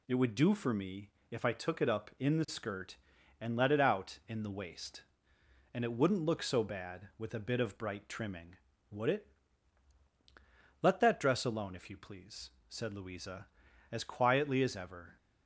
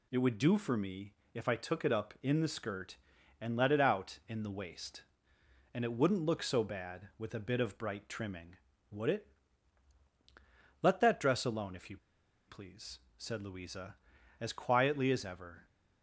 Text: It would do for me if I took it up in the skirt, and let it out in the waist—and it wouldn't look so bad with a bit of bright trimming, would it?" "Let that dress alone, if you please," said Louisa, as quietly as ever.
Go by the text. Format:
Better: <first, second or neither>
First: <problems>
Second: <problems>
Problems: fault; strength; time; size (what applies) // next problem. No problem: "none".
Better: first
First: pauses between "me" and "if"; slight; at 1.0 s; 0.22 s long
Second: pauses between "me" and "if"; slight; at 1.1 s; 0.22 s long // pauses between "you" and "please"; noticeable; at 11.9 s; 0.51 s long